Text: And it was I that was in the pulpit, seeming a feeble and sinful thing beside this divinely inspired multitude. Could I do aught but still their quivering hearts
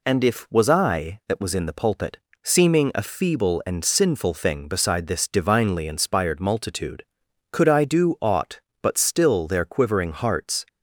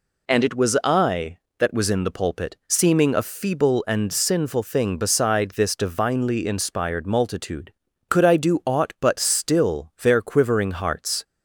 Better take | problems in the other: second | says "if" for "it"; at 0.2 s

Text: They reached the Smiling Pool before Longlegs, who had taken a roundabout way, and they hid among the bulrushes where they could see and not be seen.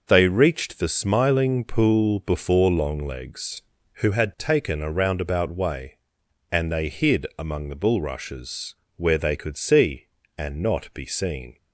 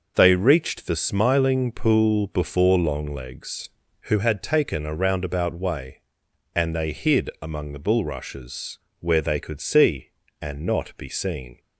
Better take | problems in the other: neither | pauses between "bulrushes" and "where"; slight; the same in both

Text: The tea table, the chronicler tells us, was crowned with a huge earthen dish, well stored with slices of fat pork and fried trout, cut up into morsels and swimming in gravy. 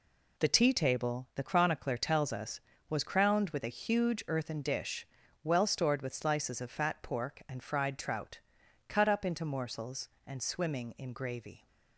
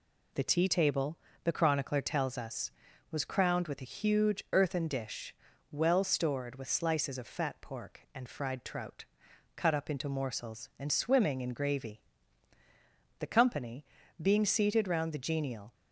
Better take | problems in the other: first | goes on to say "The company being seated round the genial"; strong; from 13.1 s on; 2.5 s long

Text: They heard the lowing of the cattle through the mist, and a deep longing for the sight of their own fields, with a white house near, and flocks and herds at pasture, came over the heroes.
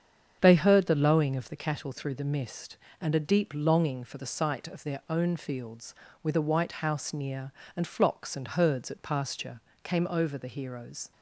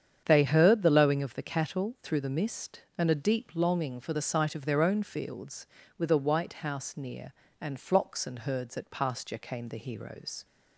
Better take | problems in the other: first | starts louder than the rest; strong; until 1.2 s; 8 dB; strong in the first // skips "over"; at 9.6 s

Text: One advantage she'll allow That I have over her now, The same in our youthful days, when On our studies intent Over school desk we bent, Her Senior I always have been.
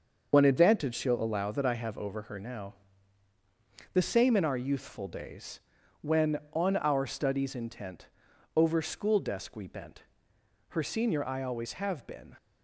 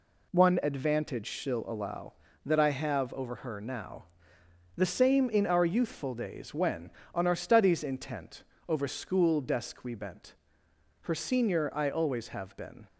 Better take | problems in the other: second | loses the start of "One"; at 0.3 s; 80 ms // starts louder than the rest; until 1.3 s; 6.5 dB // pauses between "intent" and "Over"; noticeable; at 8.0 s; 0.48 s long; slight in the second

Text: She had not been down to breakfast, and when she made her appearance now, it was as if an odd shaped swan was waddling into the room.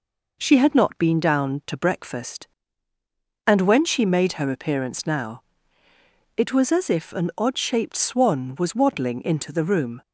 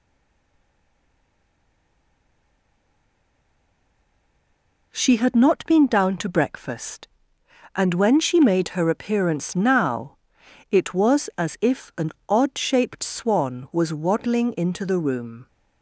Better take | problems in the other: first | stays silent before the first word; strong; until 4.9 s; 4.9 s long // pauses between "an" and "odd"; slight; at 12.1 s; 0.16 s long

